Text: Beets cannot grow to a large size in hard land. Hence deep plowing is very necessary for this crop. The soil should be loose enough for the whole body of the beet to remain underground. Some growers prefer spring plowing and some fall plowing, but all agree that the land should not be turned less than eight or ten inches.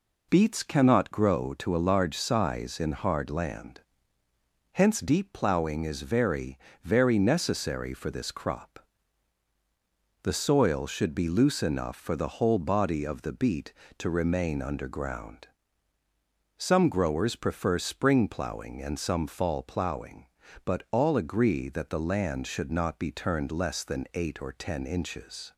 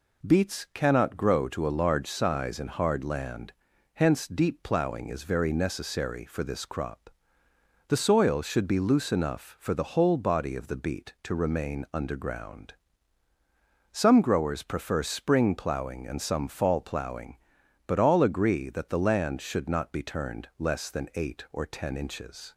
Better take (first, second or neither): second